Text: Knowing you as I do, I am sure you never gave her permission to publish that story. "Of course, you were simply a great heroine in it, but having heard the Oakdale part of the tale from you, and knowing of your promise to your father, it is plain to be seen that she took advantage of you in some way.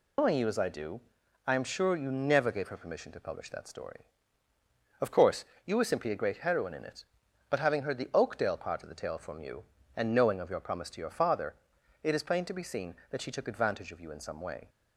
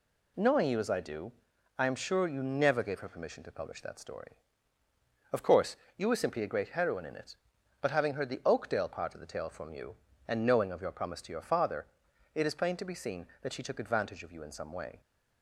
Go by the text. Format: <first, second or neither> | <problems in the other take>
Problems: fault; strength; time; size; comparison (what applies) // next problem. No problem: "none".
second | loses the start of "Knowing"; at 0.1 s; 135 ms